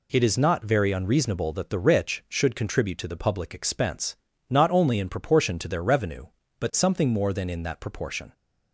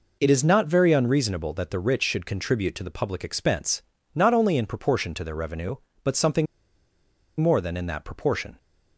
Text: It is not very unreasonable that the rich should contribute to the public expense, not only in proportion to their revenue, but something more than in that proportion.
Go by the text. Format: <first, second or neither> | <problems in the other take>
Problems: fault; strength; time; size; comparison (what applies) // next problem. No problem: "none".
first | pauses between "something" and "more"; noticeable; at 6.4 s; 0.94 s long